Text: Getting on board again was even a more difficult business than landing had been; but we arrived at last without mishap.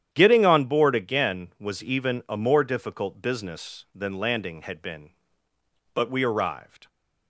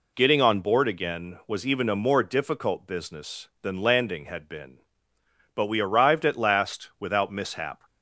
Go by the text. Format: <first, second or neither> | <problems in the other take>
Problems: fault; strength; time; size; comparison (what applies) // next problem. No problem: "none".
second | starts louder than the rest; strong; until 1.1 s; 10 dB // stops before "at last without mishap"; at 6.8 s